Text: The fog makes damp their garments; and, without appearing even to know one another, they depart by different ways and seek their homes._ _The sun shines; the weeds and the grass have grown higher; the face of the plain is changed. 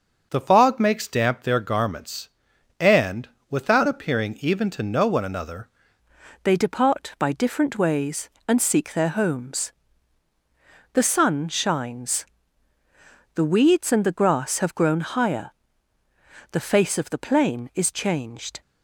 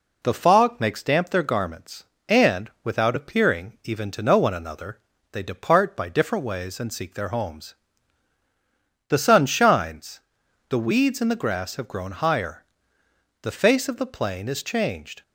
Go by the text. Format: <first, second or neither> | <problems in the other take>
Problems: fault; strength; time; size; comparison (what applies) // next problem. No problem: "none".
second | changes voice at "they"; from 6.4 s on; 12.2 s long